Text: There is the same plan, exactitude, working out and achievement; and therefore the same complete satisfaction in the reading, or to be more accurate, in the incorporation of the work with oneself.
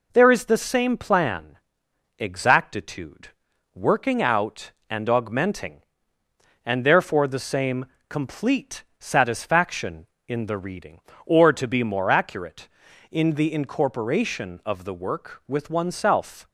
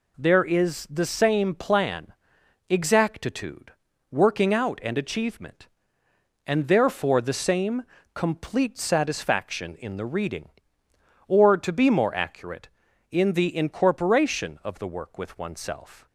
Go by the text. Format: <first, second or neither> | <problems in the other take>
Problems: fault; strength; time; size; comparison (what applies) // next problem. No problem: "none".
second | says "augmenting" for "achievement"; at 5.0 s // pauses between "same" and "complete"; slight; at 7.8 s; 0.22 s long; slight in the second // pauses between "complete" and "satisfaction"; slight; at 8.8 s; 0.16 s long